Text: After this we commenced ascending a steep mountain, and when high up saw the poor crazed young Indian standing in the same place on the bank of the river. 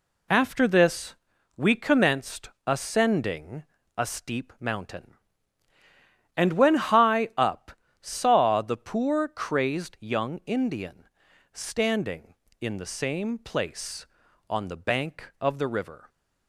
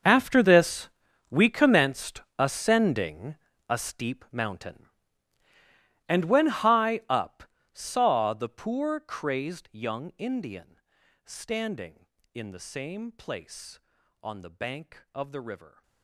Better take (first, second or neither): first